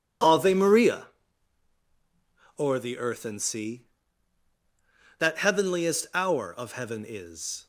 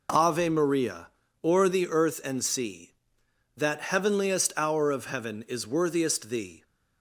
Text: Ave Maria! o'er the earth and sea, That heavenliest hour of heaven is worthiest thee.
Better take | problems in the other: second | stops before "worthiest thee"; at 7.6 s

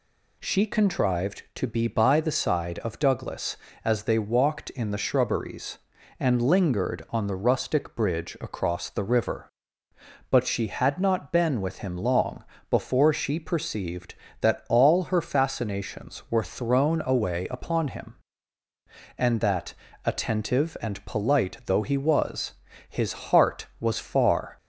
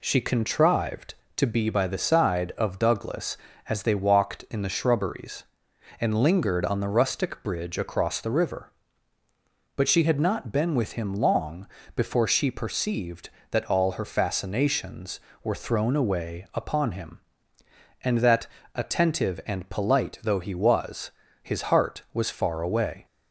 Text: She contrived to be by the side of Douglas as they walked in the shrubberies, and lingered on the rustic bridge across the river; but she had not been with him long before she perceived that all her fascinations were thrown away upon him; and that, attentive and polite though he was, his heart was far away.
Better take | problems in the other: second | pauses between "long" and "before"; slight; at 12.4 s; 0.26 s long; slight in the second // pauses between "his" and "heart"; slight; at 23.1 s; 0.18 s long // stops before "away"; at 24.5 s

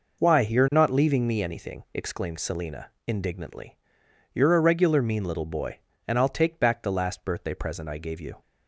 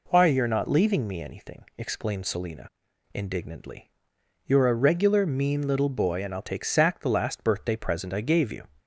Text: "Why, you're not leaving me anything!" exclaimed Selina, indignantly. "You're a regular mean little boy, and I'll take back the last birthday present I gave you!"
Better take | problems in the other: first | says "sack" for "back"; at 6.6 s

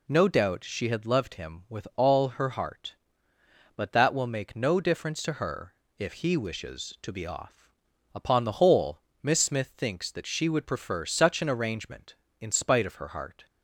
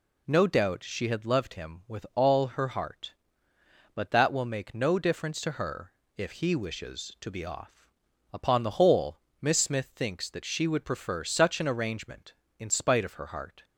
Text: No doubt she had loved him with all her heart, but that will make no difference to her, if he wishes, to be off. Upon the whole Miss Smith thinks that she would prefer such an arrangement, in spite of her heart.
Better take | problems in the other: neither | pauses between "whole" and "Miss"; slight; the same in both

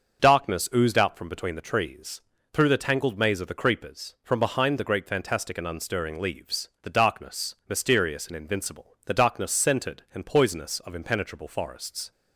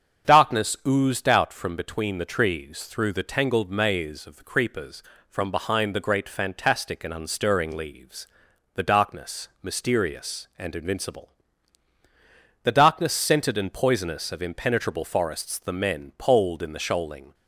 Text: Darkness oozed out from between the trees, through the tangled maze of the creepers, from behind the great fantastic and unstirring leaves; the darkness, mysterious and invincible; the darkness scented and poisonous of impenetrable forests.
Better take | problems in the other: first | starts louder than the rest; strong; until 1.3 s; 7.5 dB; also in the first // goes on to say "The men poled in the shoaling"; strong; from 15.5 s on; 1.7 s long

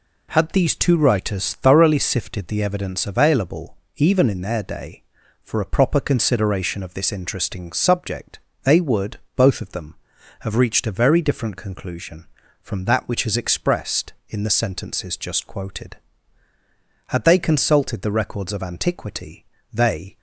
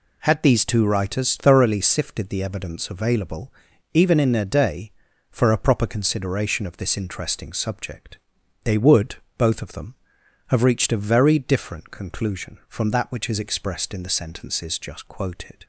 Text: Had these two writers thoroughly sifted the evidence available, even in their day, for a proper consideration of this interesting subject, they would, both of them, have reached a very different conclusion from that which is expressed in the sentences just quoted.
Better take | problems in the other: second | goes on to say "Had they consulted the records of antiquity they"; strong; from 17.0 s on; 3.1 s long

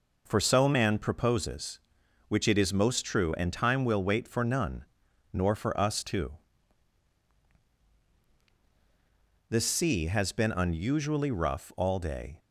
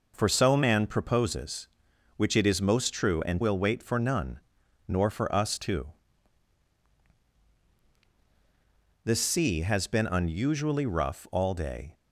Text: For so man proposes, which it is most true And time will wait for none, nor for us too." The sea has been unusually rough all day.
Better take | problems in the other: first | skips "time"; at 3.4 s

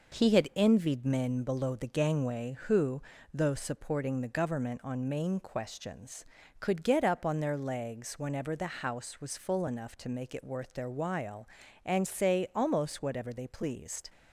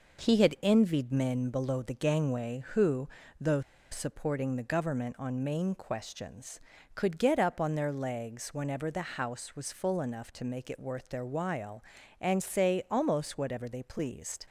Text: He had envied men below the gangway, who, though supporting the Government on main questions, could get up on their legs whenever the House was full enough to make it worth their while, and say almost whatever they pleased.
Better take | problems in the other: first | pauses between "though" and "supporting"; slight; at 3.6 s; 0.29 s long

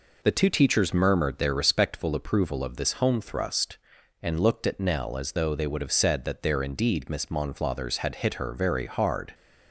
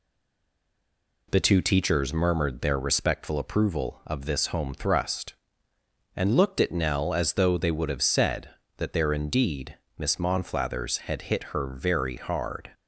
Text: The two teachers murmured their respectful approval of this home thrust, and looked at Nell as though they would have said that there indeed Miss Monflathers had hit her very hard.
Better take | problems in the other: first | stays silent before the first word; noticeable; until 1.2 s; 1.2 s long // pauses between "indeed" and "Miss"; slight; at 9.7 s; 0.18 s long

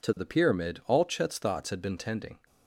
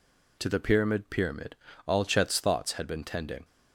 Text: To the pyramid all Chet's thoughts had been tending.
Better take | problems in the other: first | says "pyramid" twice; at 1.0 s

